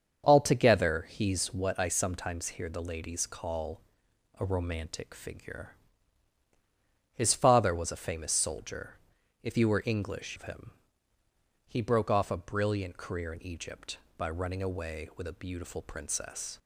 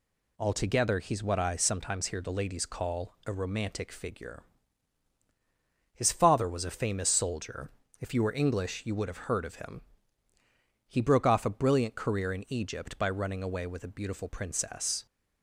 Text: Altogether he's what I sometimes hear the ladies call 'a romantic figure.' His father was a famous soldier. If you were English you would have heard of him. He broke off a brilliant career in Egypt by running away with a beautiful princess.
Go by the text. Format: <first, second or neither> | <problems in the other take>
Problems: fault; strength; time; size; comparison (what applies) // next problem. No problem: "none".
second | starts louder than the rest; until 1.2 s; 7 dB // pauses between "call" and "a"; noticeable; at 3.8 s; 0.56 s long // skips "you would have heard"; at 10.3 s